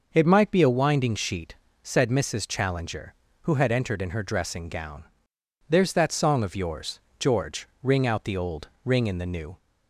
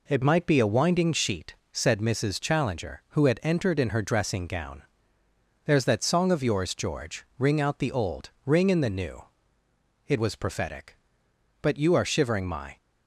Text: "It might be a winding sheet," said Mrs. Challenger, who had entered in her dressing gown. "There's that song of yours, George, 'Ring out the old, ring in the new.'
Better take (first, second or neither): first